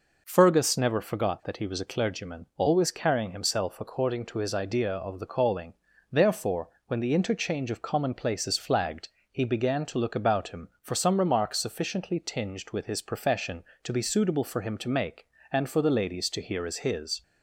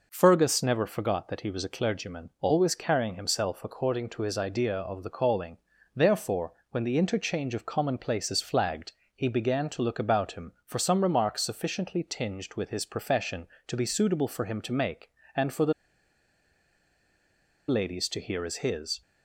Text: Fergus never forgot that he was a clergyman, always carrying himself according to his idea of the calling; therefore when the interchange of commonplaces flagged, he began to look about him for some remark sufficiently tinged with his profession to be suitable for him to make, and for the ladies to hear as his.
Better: first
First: pauses between "therefore" and "when"; slight; at 6.6 s; 0.20 s long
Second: pauses between "therefore" and "when"; slight; at 6.5 s; 0.20 s long // pauses between "the" and "ladies"; strong; at 15.7 s; 1.9 s long

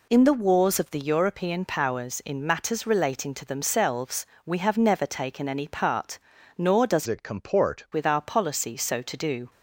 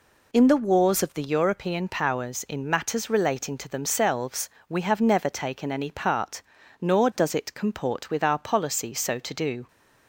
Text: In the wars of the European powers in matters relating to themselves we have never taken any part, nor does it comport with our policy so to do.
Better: second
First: pauses between "themselves" and "we"; slight; at 4.2 s; 0.18 s long // changes voice from "it" to "comport"; from 7.0 to 7.8 s; 0.8 s long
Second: pauses between "themselves" and "we"; slight; at 4.4 s; 0.18 s long

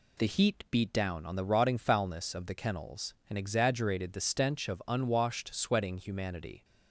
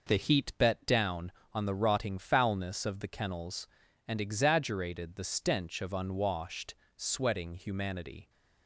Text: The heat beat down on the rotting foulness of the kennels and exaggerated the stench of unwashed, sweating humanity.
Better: first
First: none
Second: says "bet" for "beat"; at 0.5 s

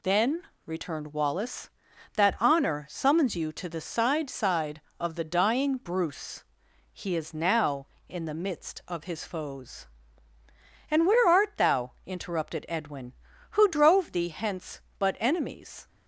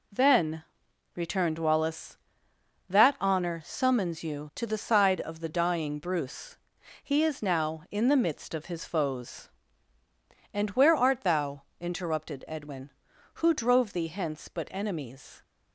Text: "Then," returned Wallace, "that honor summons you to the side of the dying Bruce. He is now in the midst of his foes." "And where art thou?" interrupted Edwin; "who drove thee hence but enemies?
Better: second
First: says "side" twice; at 4.3 s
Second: none

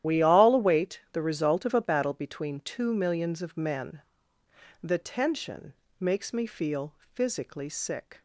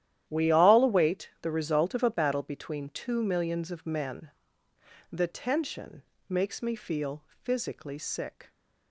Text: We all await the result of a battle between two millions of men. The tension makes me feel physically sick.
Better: second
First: loses the start of "We"; at 0.0 s; 55 ms // starts louder than the rest; strong; until 1.1 s; 11.5 dB // pauses between "tension" and "makes"; slight; at 5.7 s; 0.26 s long // pauses between "feel" and "physically"; slight; at 6.9 s; 0.22 s long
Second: starts louder than the rest; strong; until 1.2 s; 11.5 dB // pauses between "tension" and "makes"; slight; at 6.0 s; 0.26 s long // pauses between "feel" and "physically"; slight; at 7.2 s; 0.22 s long

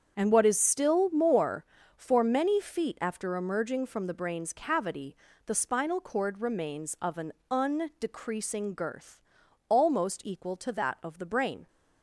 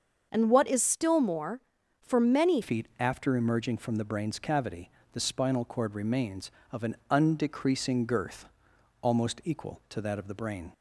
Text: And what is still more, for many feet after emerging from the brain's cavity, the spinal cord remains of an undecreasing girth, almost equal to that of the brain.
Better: first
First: starts louder than the rest; strong; until 1.1 s; 7 dB // pauses between "an" and "undecreasing"; slight; at 7.3 s; 0.18 s long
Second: starts louder than the rest; until 1.3 s; 6.5 dB // changes voice at "feet"; from 2.6 s on; 8.1 s long // pauses between "an" and "undecreasing"; slight; at 6.9 s; 0.16 s long

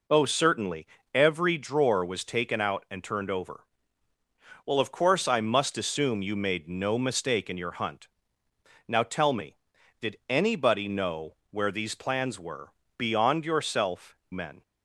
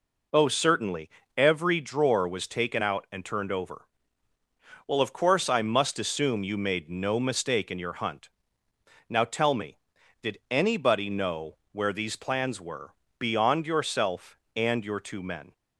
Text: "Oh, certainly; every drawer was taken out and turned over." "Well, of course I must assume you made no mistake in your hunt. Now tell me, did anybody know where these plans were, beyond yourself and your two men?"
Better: second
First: pauses between "know" and "where"; slight; at 11.3 s; 0.16 s long // skips "and your two"; at 14.2 s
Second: pauses between "know" and "where"; slight; at 11.5 s; 0.16 s long

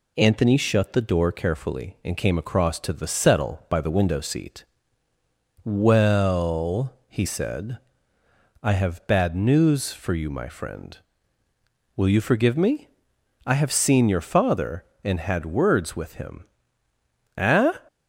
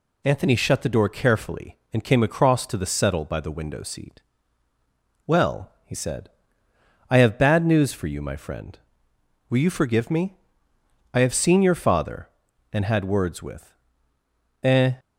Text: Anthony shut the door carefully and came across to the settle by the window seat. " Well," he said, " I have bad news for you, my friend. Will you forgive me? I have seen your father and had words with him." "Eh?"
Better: first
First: none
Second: skips "him"; at 14.1 s

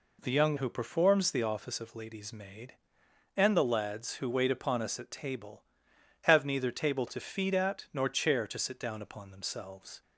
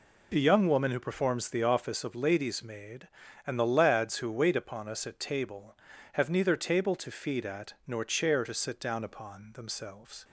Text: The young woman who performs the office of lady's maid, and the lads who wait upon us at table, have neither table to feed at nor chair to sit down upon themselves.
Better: second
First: skips "woman"; at 0.5 s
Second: none

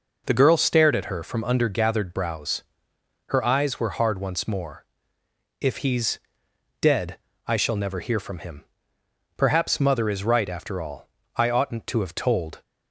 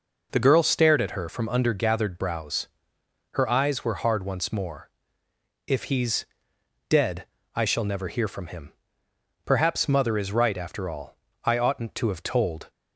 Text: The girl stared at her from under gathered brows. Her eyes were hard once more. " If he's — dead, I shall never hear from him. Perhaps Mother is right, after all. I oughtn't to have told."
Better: neither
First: none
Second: none

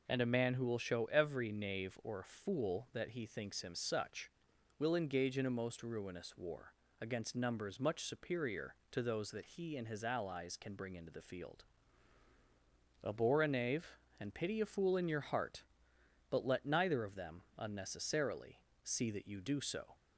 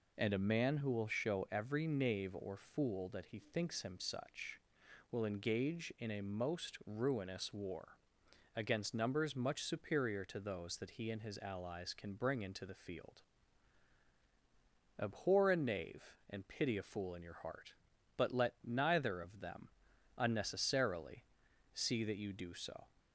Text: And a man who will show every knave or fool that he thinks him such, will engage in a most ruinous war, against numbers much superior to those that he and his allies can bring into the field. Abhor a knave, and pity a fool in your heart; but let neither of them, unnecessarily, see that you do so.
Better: neither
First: none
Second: none

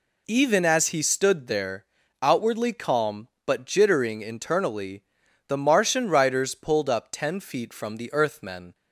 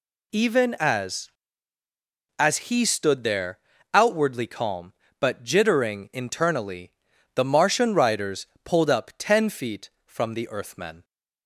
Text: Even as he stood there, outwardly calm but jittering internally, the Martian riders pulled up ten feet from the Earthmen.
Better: first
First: none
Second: says "as" twice; at 2.3 s // pauses between "riders" and "pulled"; slight; at 8.4 s; 0.18 s long

